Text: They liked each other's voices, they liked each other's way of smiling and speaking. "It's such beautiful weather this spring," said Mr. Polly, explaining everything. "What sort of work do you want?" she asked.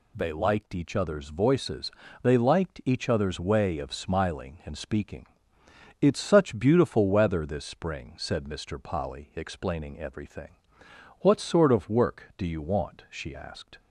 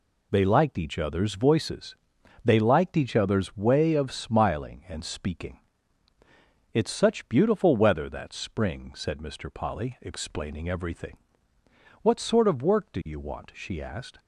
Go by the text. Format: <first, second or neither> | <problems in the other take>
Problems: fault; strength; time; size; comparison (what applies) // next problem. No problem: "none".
first | says "that" for "this"; at 8.0 s